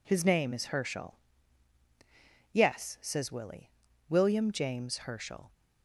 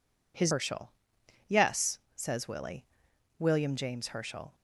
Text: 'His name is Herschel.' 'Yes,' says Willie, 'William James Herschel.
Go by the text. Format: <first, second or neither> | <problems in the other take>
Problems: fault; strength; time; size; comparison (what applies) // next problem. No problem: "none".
first | skips "name is"; at 0.5 s